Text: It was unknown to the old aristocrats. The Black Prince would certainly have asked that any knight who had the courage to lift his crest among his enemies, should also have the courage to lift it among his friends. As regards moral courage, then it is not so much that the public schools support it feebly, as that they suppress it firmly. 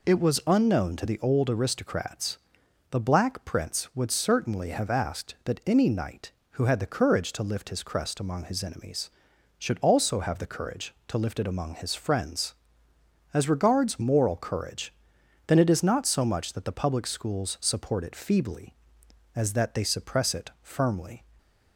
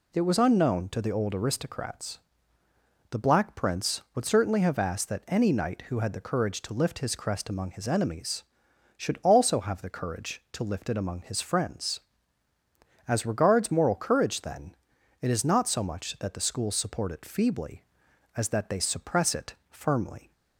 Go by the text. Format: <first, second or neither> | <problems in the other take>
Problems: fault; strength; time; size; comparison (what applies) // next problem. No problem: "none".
first | pauses between "then" and "it"; at 14.7 s; 0.44 s long // skips "public"; at 16.3 s // pauses between "it" and "firmly"; slight; at 19.5 s; 0.16 s long